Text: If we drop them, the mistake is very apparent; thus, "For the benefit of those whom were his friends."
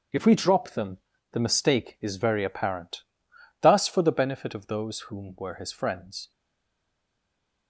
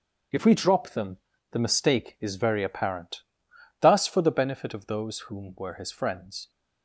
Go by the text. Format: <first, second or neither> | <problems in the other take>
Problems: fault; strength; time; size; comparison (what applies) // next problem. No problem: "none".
second | stays silent after the last word; noticeable; from 6.3 s on; 1.3 s long